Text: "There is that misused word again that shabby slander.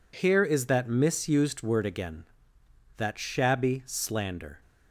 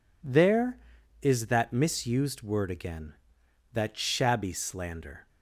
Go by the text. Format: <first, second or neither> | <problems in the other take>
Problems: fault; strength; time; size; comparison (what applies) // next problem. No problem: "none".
second | says "Here" for "There"; at 0.1 s